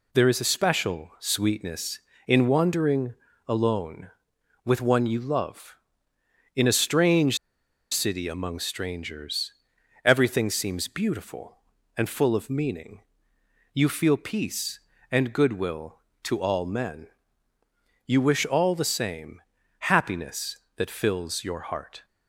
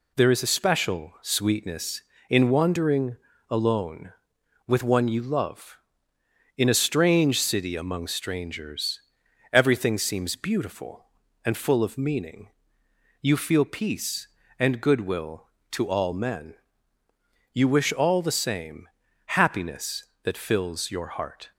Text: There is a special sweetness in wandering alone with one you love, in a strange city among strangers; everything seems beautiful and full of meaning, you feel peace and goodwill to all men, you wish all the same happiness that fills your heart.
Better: second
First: pauses between "wandering" and "alone"; slight; at 3.1 s; 0.34 s long // pauses between "strange" and "city"; noticeable; at 7.3 s; 0.55 s long // pauses between "same" and "happiness"; at 19.4 s; 0.38 s long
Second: pauses between "wandering" and "alone"; slight; at 3.1 s; 0.34 s long // pauses between "same" and "happiness"; at 18.8 s; 0.38 s long

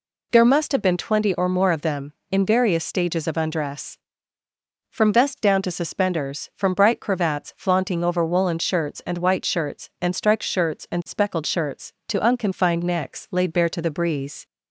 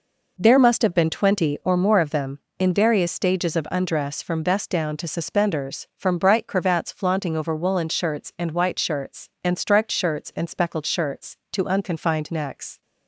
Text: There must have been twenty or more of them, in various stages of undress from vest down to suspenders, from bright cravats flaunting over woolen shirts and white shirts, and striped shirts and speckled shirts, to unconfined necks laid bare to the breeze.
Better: first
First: none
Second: stops before "laid bare to the breeze"; at 12.8 s

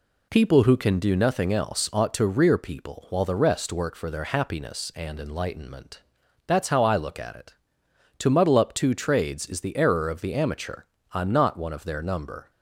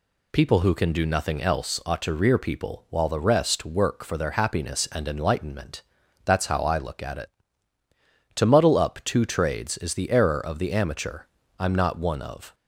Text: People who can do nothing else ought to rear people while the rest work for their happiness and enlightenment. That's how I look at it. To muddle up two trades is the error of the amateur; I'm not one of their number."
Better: first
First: none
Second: stops before "their number"; at 12.5 s

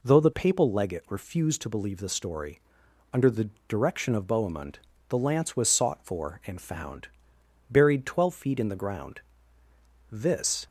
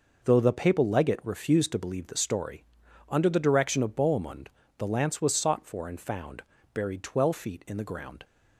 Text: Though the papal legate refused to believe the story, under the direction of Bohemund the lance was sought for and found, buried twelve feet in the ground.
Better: second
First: pauses between "the" and "direction"; slight; at 3.4 s; 0.20 s long // pauses between "Bohemund" and "the"; slight; at 4.7 s; 0.28 s long // goes on to say "This"; from 10.1 s on; 0.56 s long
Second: pauses between "Bohemund" and "the"; slight; at 4.4 s; 0.30 s long

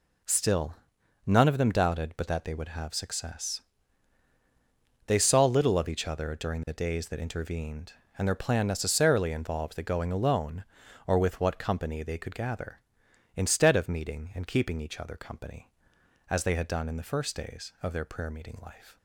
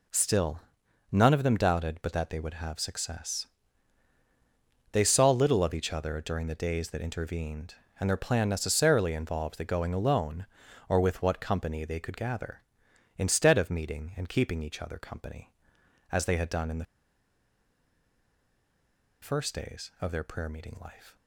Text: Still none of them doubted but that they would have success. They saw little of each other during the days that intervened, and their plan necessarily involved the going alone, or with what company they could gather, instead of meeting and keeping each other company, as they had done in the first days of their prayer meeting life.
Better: first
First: pauses between "Still" and "none"; noticeable; at 0.7 s; 0.50 s long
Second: pauses between "Still" and "none"; noticeable; at 0.6 s; 0.50 s long // pauses between "the" and "first"; strong; at 16.8 s; 2.3 s long

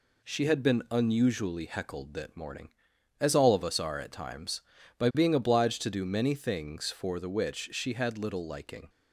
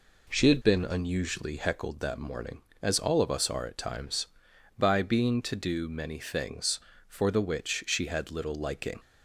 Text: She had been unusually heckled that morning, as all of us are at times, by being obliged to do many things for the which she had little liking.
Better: first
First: none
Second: skips "obliged"; at 5.4 s

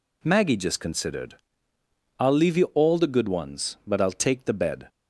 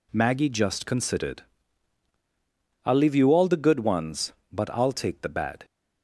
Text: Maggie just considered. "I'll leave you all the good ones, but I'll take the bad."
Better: second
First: says "bed" for "bad"; at 4.5 s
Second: none

